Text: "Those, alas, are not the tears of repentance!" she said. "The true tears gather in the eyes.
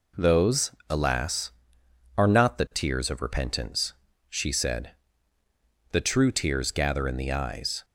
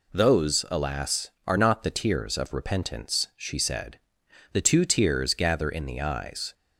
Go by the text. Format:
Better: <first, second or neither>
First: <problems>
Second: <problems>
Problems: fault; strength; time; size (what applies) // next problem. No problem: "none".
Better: first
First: none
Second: says "two" for "true"; at 4.6 s